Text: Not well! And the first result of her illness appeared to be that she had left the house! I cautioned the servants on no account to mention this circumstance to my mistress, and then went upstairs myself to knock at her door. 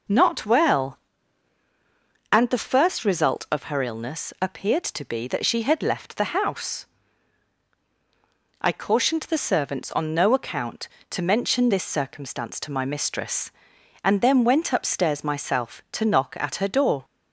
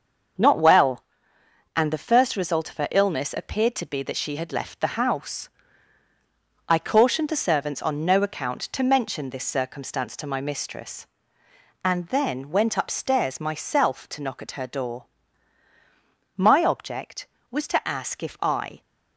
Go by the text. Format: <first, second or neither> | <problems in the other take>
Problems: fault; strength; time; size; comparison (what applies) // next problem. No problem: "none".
first | starts louder than the rest; until 2.0 s; 6.5 dB // goes on to say "My object was to ask if I"; strong; from 16.3 s on; 2.4 s long